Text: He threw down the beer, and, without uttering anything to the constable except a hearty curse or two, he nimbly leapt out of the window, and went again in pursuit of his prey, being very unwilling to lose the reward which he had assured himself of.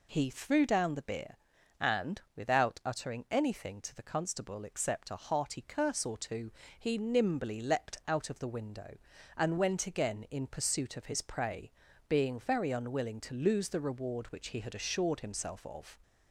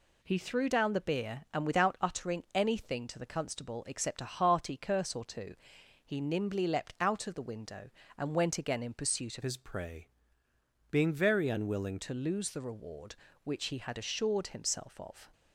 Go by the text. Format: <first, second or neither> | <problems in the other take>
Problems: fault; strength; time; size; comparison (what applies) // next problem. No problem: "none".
first | changes voice from "his" to "unwilling"; from 9.4 to 12.0 s; 2.6 s long